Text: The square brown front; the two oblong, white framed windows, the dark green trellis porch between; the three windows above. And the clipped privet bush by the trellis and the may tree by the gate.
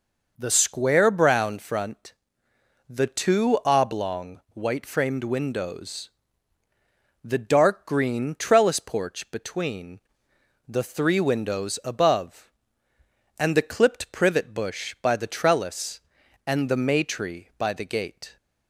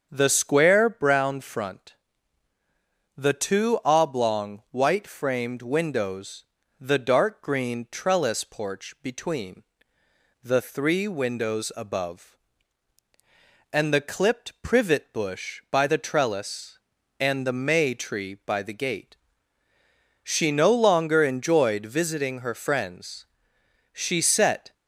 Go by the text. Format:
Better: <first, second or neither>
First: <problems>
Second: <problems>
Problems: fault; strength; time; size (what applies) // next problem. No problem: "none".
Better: first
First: none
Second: starts louder than the rest; until 1.1 s; 7 dB // goes on to say "She no longer enjoyed visiting her friends She set"; strong; from 20.2 s on; 4.5 s long